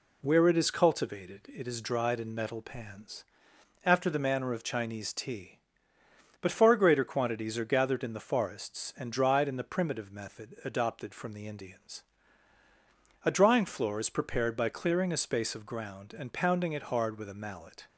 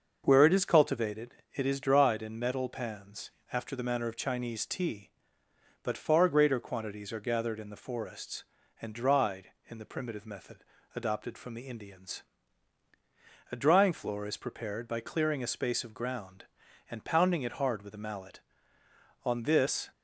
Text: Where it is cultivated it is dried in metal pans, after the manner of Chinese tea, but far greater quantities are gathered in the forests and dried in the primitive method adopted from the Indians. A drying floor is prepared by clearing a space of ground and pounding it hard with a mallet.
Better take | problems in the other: first | starts louder than the rest; until 1.2 s; 6.5 dB // pauses between "cultivated" and "it"; slight; at 1.3 s; 0.18 s long // pauses between "method" and "adopted"; slight; at 10.6 s; 0.30 s long // goes on to say "On this"; noticeable; from 19.2 s on; 0.66 s long

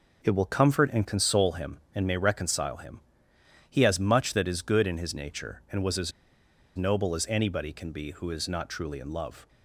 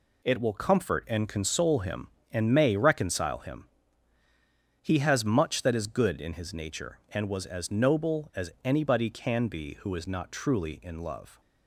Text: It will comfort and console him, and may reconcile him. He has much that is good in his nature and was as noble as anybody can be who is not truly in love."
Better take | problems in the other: second | pauses between "as" and "noble"; noticeable; at 6.1 s; 0.65 s long

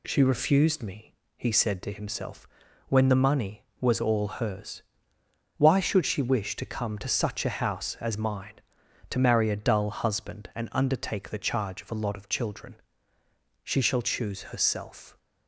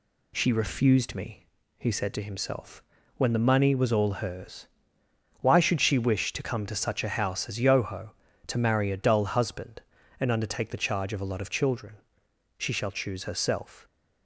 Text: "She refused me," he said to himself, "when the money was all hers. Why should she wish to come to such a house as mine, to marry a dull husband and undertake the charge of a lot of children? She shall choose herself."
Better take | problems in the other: first | says "yoho" for "mine"; at 7.6 s

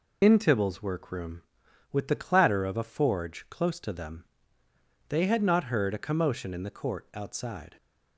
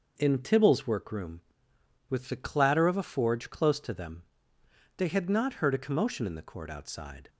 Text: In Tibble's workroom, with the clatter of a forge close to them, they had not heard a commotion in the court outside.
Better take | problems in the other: second | loses the start of "In"; at 0.2 s; 80 ms

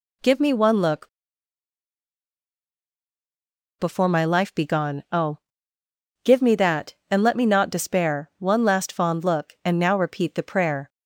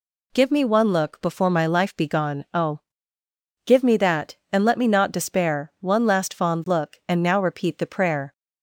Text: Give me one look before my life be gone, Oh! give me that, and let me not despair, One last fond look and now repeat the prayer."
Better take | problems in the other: second | pauses between "look" and "before"; strong; at 1.0 s; 2.7 s long

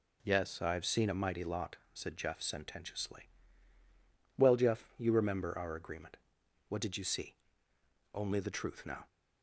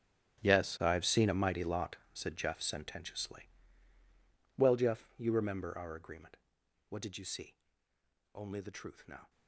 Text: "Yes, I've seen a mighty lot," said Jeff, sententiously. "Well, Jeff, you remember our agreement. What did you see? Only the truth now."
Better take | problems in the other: first | gets quieter; strong; throughout; 16 dB

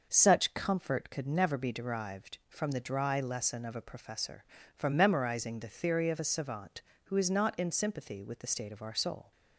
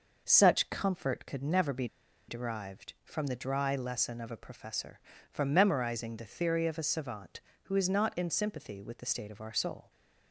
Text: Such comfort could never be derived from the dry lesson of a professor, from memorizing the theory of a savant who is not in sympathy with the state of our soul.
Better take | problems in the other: first | pauses between "be" and "derived"; at 1.8 s; 0.42 s long

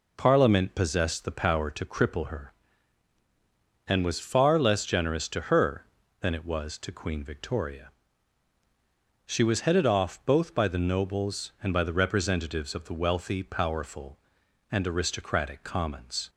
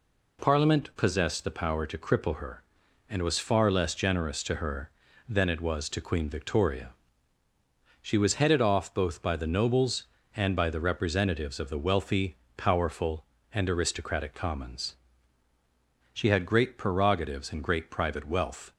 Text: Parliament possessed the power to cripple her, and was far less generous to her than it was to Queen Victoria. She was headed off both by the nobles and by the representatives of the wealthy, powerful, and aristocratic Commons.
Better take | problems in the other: first | goes on to say "She had great prerogatives and great private wealth"; strong; from 16.1 s on; 2.5 s long

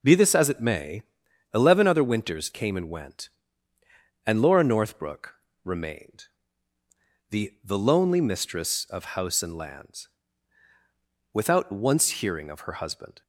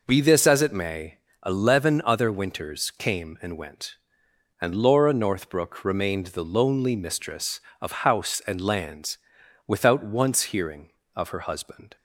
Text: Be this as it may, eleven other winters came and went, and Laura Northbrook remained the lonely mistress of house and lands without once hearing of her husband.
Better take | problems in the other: second | pauses between "Northbrook" and "remained"; slight; at 5.3 s; 0.28 s long // pauses between "remained" and "the"; at 6.2 s; 1.0 s long // says "the" twice; at 7.6 s // pauses between "lands" and "without"; at 10.0 s; 1.2 s long; noticeable in the second

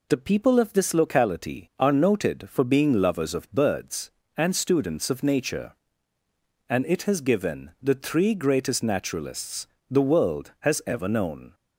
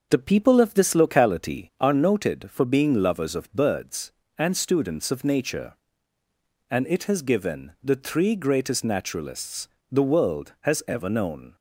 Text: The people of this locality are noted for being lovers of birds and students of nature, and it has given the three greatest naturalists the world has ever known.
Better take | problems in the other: first | starts louder than the rest; until 1.9 s; 6 dB // pauses between "naturalists" and "the"; slight; at 9.6 s; 0.22 s long; slight in the first

